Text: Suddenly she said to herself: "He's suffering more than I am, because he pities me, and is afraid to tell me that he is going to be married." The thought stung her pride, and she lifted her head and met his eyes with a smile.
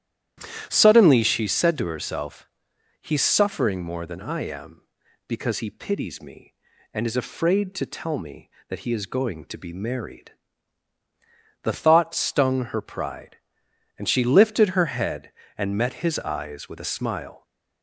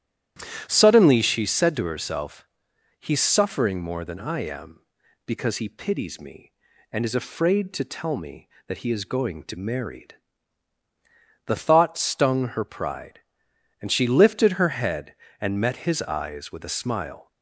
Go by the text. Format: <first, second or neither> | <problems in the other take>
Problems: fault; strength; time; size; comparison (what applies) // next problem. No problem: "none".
first | starts louder than the rest; strong; until 1.7 s; 11.5 dB; strong in the first // skips "be"; at 9.5 s